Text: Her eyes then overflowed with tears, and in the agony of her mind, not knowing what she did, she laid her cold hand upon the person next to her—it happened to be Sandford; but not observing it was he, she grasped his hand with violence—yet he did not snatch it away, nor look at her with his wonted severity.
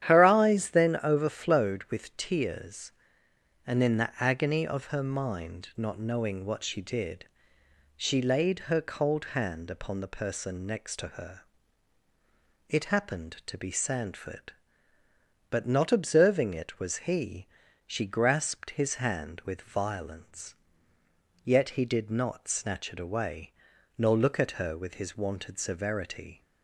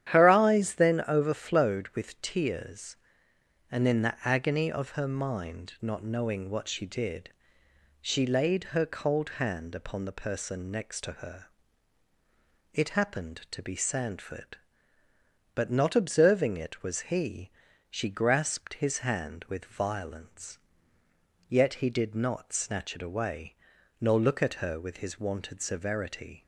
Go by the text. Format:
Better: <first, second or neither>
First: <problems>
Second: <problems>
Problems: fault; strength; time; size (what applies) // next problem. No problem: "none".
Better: neither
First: starts louder than the rest; strong; until 1.1 s; 10.5 dB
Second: starts louder than the rest; strong; until 1.1 s; 10.5 dB